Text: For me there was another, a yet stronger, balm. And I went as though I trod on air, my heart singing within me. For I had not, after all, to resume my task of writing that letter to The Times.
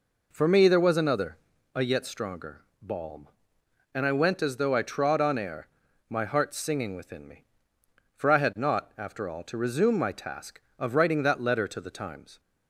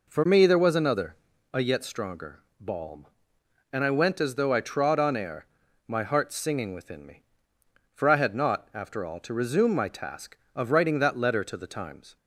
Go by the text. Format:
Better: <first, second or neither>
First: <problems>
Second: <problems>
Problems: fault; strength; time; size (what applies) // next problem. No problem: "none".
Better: neither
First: none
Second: none